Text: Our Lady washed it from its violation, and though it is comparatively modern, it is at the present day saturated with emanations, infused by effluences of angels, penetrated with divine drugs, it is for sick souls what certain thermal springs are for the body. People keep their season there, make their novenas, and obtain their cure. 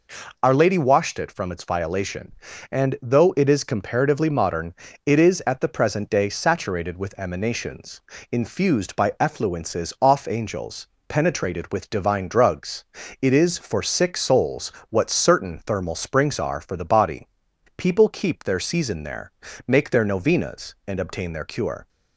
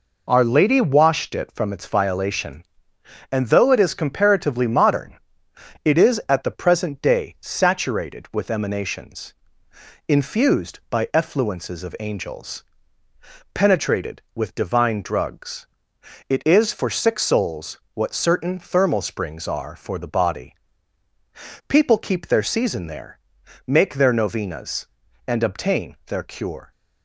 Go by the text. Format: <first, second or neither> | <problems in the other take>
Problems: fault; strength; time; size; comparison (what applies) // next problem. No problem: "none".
second | says "off" for "of"; at 10.0 s // pauses between "souls" and "what"; slight; at 14.7 s; 0.20 s long; slight in the second